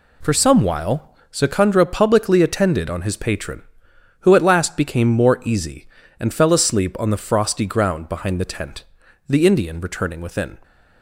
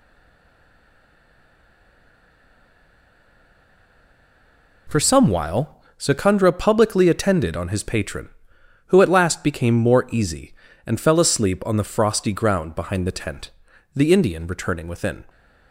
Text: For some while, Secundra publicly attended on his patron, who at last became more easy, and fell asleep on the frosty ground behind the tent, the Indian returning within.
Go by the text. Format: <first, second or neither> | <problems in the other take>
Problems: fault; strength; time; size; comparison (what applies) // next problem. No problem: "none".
first | stays silent before the first word; strong; until 4.8 s; 4.8 s long